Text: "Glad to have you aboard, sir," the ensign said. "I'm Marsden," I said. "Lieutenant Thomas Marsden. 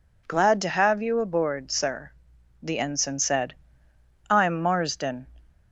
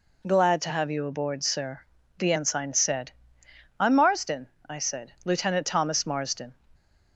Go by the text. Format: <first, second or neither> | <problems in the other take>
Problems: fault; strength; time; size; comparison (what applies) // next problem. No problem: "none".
second | stops before "I said Lieutenant Thomas Marsden"; at 5.4 s